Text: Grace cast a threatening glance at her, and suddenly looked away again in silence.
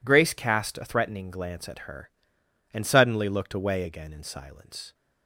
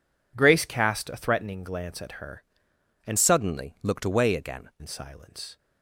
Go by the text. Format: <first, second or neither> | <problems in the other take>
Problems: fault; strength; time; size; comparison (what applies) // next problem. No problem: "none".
first | changes voice from "suddenly" to "again"; from 3.1 to 4.7 s; 1.6 s long